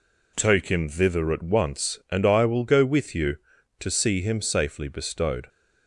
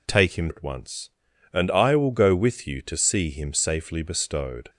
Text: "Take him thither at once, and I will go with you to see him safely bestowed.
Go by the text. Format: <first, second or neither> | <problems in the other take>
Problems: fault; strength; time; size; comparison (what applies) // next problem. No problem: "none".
first | skips "thither"; at 0.4 s